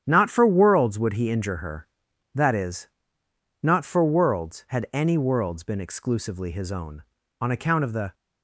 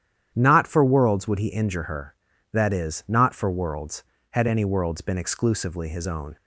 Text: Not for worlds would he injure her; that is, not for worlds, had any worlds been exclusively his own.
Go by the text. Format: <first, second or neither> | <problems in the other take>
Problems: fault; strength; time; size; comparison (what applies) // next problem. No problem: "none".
second | starts louder than the rest; strong; until 1.0 s; 10 dB; strong in the second // goes on to say "On account of the"; noticeable; from 7.4 s on; 0.72 s long